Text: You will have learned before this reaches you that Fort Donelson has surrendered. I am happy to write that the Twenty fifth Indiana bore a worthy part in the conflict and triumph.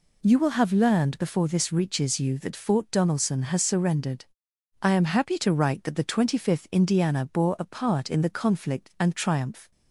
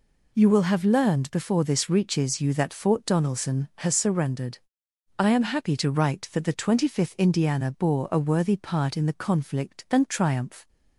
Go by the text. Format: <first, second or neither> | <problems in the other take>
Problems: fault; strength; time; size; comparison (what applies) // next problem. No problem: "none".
second | skips "worthy"; at 7.6 s